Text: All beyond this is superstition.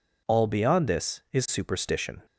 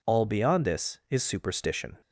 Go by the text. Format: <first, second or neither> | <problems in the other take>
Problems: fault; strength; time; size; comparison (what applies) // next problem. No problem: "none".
neither | none